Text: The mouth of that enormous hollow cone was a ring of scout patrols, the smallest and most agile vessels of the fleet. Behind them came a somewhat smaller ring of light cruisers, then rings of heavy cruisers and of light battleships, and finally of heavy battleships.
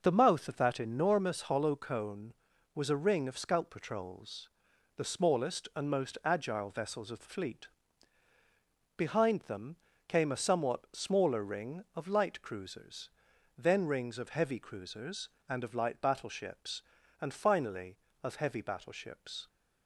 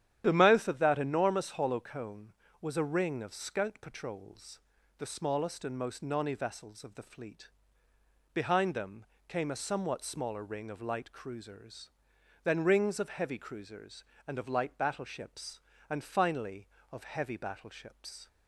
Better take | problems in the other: first | starts louder than the rest; strong; until 1.2 s; 10.5 dB // says "nonny" for "agile"; at 6.0 s // pauses between "them" and "came"; slight; at 9.0 s; 0.22 s long; slight in the first

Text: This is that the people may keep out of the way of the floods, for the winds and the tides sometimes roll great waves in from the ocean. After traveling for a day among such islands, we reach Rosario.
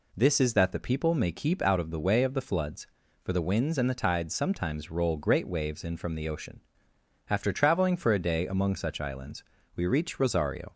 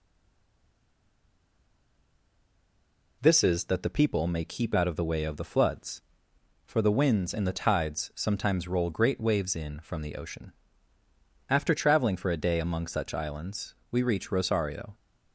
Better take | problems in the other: first | stays silent before the first word; strong; until 3.2 s; 3.2 s long

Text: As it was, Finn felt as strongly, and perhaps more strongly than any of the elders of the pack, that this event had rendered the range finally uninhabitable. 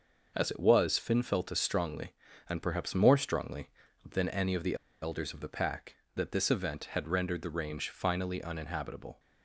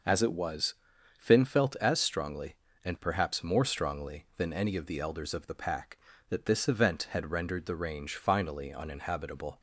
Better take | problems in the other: second | pauses between "the" and "elders"; slight; at 4.7 s; 0.27 s long

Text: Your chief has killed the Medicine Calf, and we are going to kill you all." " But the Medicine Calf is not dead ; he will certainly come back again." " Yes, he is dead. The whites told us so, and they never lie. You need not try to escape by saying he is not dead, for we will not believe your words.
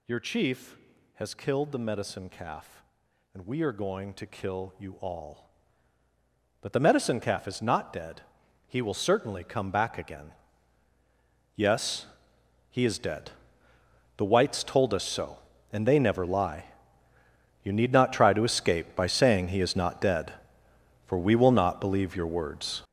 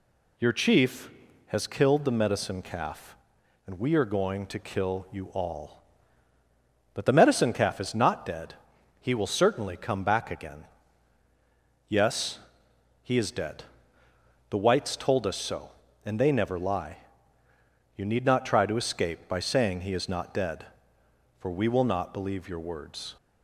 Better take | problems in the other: second | gets louder; strong; throughout; 14 dB

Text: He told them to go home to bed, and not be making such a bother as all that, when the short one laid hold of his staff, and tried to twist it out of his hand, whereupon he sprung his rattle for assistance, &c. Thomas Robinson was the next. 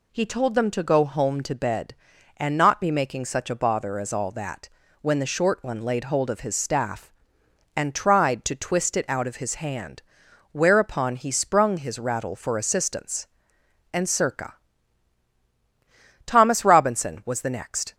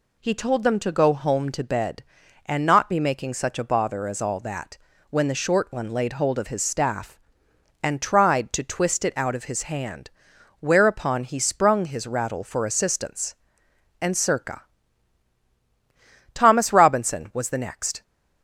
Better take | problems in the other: neither | none

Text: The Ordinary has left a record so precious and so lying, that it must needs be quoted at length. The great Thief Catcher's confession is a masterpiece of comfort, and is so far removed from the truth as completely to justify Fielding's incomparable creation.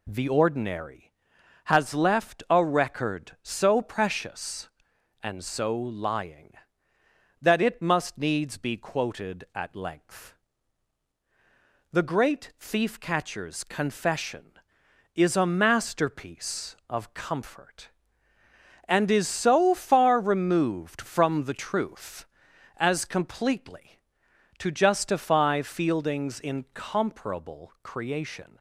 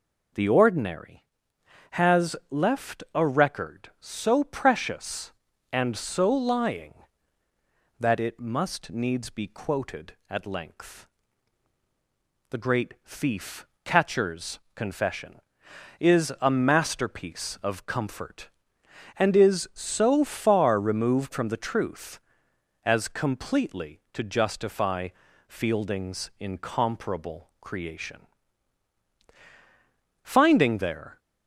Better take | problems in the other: first | pauses between "Thief" and "Catcher's"; slight; at 13.6 s; 0.20 s long // pauses between "Catcher's" and "confession"; slight; at 14.5 s; 0.16 s long // pauses between "justify" and "Fielding's"; at 25.0 s; 0.38 s long // goes on to say "Finding there"; noticeable; from 30.2 s on; 0.94 s long

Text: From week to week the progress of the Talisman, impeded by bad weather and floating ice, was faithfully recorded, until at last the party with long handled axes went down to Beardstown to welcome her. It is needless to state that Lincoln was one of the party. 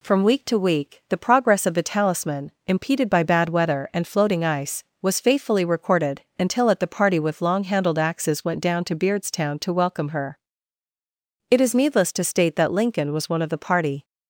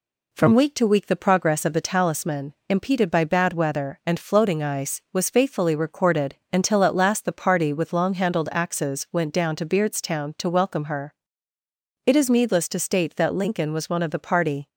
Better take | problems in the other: second | skips "last"; at 6.8 s

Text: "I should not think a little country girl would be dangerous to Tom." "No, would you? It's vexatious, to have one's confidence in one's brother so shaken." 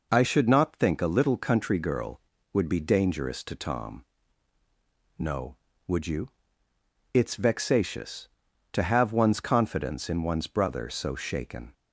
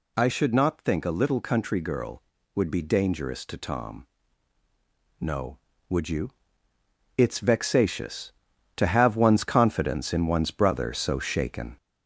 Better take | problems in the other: first | gets louder; slight; throughout; 3 dB

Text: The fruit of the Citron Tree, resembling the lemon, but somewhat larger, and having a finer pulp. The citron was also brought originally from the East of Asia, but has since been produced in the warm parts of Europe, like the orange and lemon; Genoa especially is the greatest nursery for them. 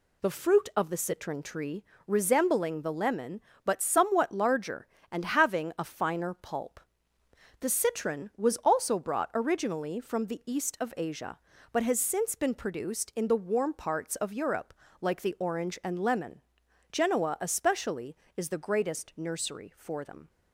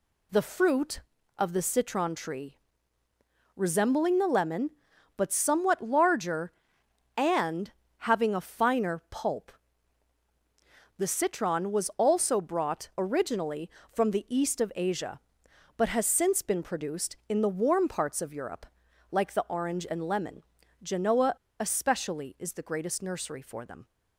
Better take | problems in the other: first | pauses between "and" and "having"; slight; at 7.7 s; 0.30 s long // pauses between "Genoa" and "especially"; slight; at 21.3 s; 0.27 s long

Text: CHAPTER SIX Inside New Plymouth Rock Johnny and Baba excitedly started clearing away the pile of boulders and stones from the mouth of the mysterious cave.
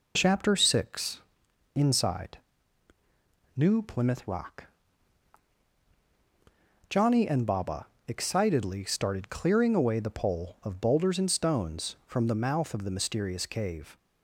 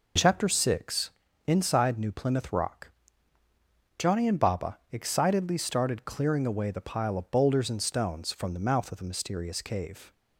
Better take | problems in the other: second | pauses between "SIX" and "Inside"; noticeable; at 1.2 s; 0.54 s long; slight in the second // pauses between "Inside" and "New"; at 2.3 s; 1.1 s long // pauses between "Rock" and "Johnny"; strong; at 4.6 s; 2.2 s long; also in the second // pauses between "Baba" and "excitedly"; slight; at 7.8 s; 0.20 s long; slight in the second // says "pole" for "pile"; at 10.1 s

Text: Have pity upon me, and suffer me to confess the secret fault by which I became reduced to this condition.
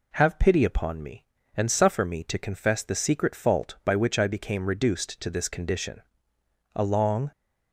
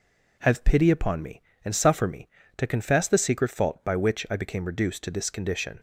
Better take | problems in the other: second | goes on to say "A long"; from 6.7 s on; 0.56 s long

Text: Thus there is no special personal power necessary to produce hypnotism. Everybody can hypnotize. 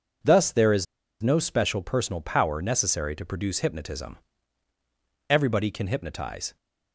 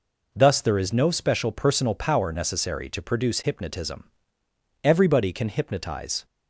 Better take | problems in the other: second | pauses between "is" and "no"; at 0.8 s; 0.37 s long

